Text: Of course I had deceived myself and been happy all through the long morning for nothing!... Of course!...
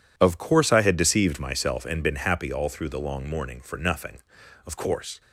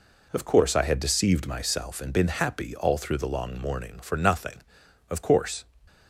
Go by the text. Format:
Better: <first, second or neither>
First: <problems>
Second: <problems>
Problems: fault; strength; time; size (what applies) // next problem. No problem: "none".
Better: neither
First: none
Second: none